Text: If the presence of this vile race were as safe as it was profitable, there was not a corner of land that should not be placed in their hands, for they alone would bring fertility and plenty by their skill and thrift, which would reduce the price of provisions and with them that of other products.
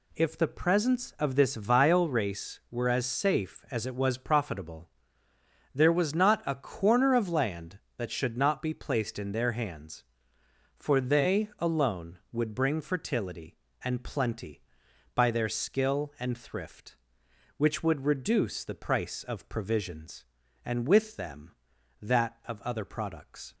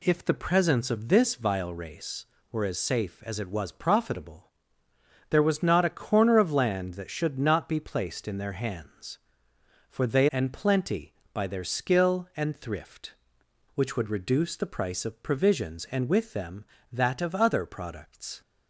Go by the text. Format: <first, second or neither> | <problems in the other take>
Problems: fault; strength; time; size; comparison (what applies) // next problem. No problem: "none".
first | skips "alone would bring fertility"; at 10.2 s